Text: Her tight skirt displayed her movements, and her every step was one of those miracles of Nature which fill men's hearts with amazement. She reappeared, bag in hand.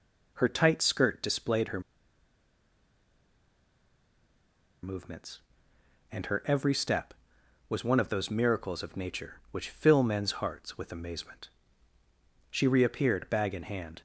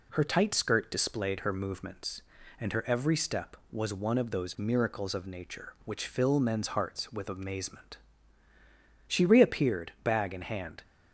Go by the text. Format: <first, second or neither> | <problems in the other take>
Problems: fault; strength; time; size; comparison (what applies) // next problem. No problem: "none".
second | pauses between "her" and "movements"; strong; at 1.8 s; 3.0 s long